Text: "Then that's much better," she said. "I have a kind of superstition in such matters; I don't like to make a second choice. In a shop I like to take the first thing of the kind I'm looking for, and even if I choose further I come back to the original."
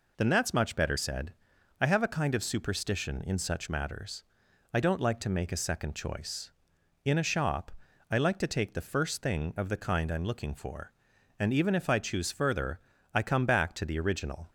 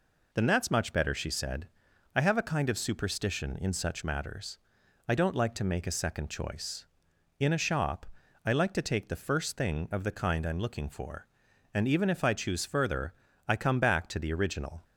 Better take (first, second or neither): second